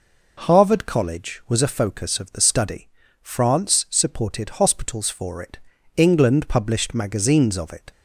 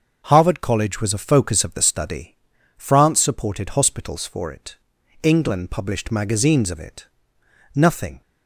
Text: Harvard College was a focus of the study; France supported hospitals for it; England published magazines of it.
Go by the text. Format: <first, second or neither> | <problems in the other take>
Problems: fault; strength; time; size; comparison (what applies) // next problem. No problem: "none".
first | starts louder than the rest; until 1.2 s; 6.5 dB // goes on to say "Nothing"; slight; from 7.7 s on; 0.46 s long